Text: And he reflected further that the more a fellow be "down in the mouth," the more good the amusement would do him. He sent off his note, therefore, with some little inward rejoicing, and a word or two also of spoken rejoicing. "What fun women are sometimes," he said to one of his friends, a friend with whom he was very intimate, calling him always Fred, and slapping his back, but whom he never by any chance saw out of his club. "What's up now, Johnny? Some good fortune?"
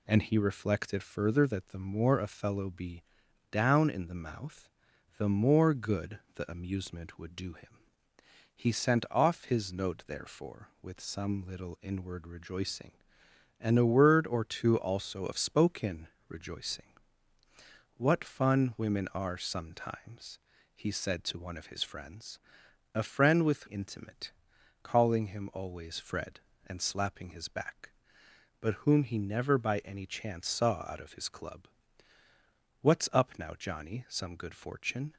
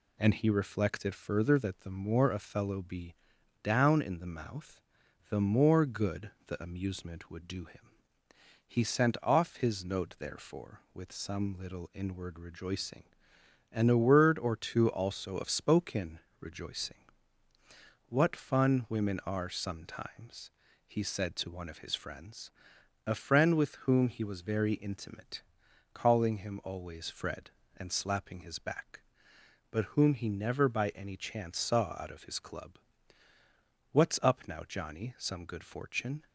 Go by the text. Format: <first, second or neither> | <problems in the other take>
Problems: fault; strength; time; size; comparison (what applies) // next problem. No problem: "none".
second | pauses between "be" and "down"; noticeable; at 3.0 s; 0.48 s long; noticeable in the second // pauses between "spoken" and "rejoicing"; slight; at 16.0 s; 0.20 s long; slight in the second // skips "whom he was very"; at 23.6 s